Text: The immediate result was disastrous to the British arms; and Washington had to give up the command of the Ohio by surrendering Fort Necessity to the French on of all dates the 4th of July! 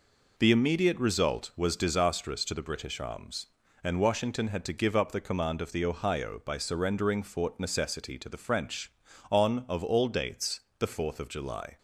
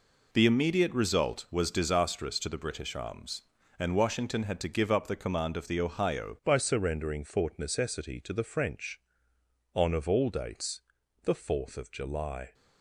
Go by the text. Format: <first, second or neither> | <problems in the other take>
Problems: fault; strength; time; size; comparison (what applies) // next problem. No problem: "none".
first | changes voice at "by"; from 6.4 s on; 6.1 s long // pauses between "dates" and "the"; at 10.8 s; 0.40 s long; slight in the first